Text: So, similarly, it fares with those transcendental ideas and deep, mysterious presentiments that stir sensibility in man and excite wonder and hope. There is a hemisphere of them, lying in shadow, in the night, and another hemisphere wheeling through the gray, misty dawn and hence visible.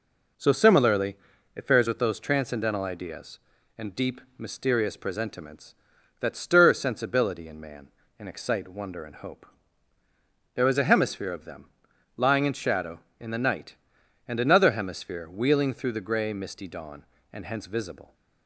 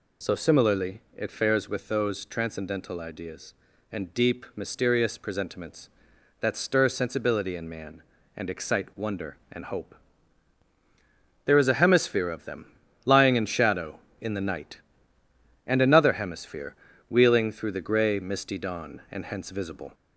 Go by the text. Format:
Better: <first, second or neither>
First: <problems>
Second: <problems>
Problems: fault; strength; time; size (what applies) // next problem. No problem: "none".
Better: first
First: none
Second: gets louder; slight; throughout; 2.5 dB // pauses between "hemisphere" and "wheeling"; slight; at 16.7 s; 0.36 s long